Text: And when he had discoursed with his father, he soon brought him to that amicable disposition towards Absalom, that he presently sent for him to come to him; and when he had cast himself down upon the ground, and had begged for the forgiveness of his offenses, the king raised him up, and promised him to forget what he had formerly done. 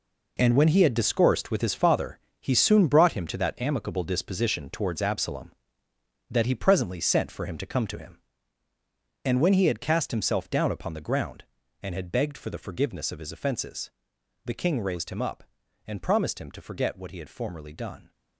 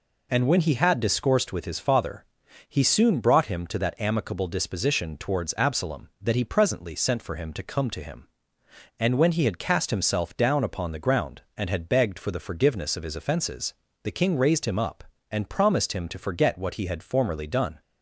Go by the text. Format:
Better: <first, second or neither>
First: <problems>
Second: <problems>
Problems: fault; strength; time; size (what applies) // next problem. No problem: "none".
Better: second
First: gets quieter; strong; throughout; 10.5 dB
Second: none